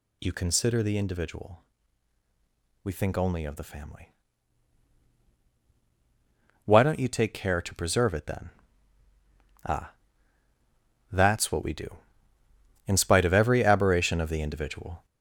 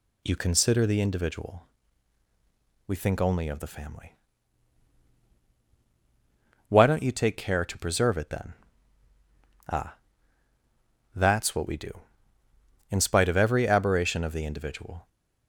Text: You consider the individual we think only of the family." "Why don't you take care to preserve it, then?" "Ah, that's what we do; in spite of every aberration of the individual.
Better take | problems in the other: second | gets louder; noticeable; throughout; 5.5 dB // pauses between "individual" and "we"; at 1.6 s; 1.2 s long; also in the second

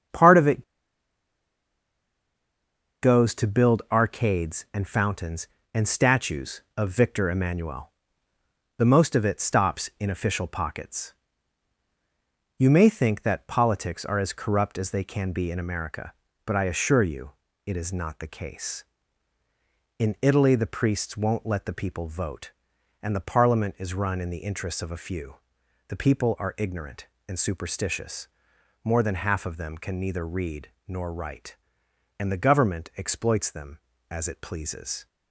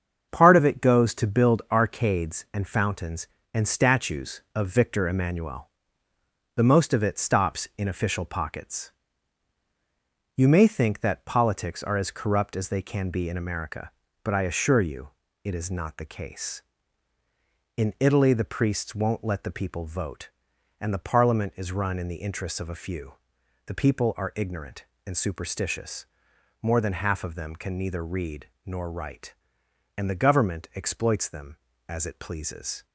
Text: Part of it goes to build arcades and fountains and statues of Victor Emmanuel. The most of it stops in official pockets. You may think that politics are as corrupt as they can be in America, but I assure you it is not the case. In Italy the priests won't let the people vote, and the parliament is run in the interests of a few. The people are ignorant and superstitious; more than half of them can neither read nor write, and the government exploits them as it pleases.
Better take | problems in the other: second | starts louder than the rest; strong; until 3.5 s; 7.5 dB; also in the second // pauses between "it" and "goes"; strong; at 0.6 s; 2.3 s long // pauses between "you" and "it"; slight; at 17.3 s; 0.34 s long; slight in the second // pauses between "read" and "nor"; slight; at 30.6 s; 0.18 s long; slight in the second

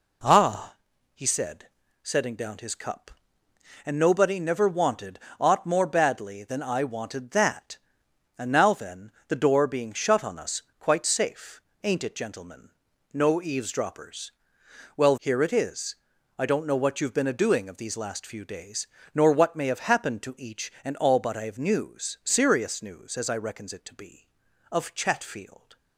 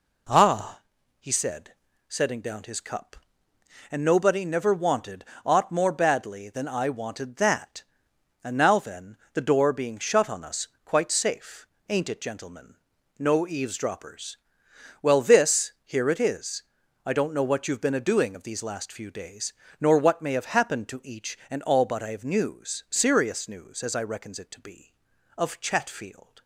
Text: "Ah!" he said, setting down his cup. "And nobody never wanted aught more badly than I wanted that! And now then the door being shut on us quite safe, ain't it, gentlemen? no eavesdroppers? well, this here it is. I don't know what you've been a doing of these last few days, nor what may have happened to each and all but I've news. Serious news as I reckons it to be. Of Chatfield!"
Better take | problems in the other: second | pauses between "wanted" and "aught"; slight; at 5.1 s; 0.22 s long; slight in the second // pauses between "then" and "the"; slight; at 9.0 s; 0.16 s long; slight in the second // pauses between "us" and "quite"; slight; at 10.6 s; 0.16 s long; slight in the second // skips "this"; at 15.1 s

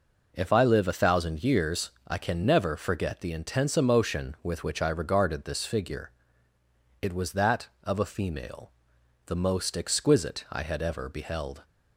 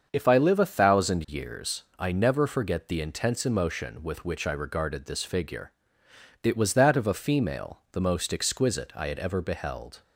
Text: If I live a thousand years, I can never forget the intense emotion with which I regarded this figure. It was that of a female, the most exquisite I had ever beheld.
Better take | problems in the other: first | starts louder than the rest; until 1.1 s; 7 dB // skips "can"; at 2.1 s

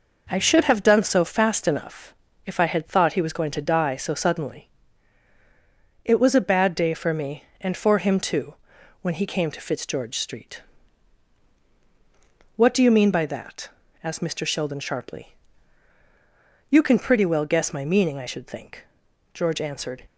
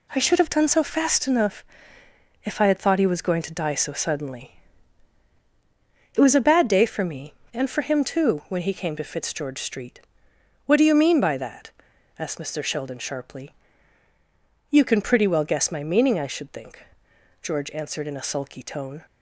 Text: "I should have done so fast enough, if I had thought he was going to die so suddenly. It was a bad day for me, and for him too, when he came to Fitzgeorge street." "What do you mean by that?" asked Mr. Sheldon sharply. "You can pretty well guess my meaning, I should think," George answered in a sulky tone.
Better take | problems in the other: second | stops before "in a sulky tone"; at 20.0 s

